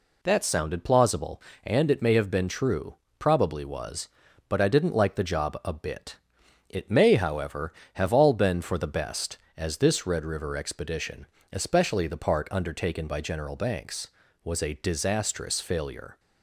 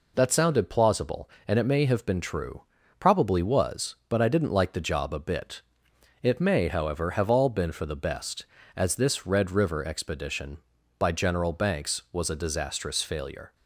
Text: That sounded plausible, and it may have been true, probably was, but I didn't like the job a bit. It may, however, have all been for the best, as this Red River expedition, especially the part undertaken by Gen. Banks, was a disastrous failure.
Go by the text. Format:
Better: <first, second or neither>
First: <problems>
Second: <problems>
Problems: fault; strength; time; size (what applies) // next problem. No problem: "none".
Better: first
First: none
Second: skips "especially the part undertaken"; at 10.7 s